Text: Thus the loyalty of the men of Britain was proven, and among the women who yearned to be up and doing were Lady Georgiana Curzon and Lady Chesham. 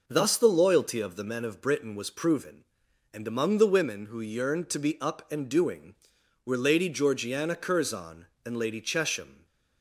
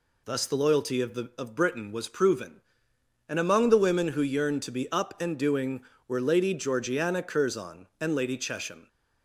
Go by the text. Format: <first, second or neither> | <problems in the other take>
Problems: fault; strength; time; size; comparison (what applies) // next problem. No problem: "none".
first | skips "men"; at 1.3 s